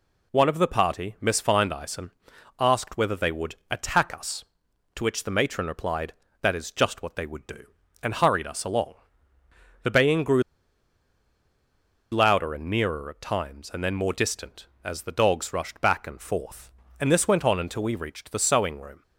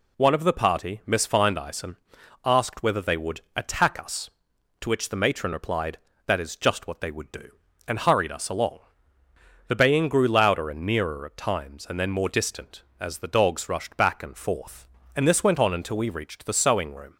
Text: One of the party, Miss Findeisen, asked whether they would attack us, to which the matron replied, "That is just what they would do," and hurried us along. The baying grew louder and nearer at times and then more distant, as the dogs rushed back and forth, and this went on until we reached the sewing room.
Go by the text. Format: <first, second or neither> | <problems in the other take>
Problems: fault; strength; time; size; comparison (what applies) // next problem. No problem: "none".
second | pauses between "would" and "attack"; slight; at 3.5 s; 0.16 s long; slight in the second // pauses between "grew" and "louder"; strong; at 10.4 s; 1.6 s long